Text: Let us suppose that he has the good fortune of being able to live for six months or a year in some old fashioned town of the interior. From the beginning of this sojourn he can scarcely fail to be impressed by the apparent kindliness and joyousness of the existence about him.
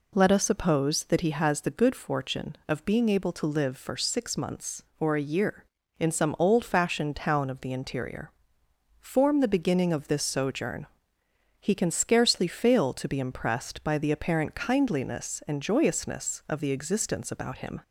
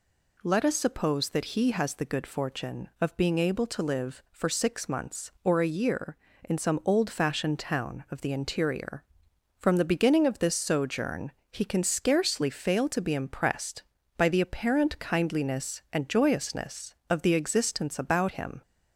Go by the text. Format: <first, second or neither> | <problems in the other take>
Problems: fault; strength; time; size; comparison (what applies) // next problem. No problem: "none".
second | says "Form" for "From"; at 8.9 s // pauses between "sojourn" and "he"; noticeable; at 10.8 s; 0.74 s long; slight in the second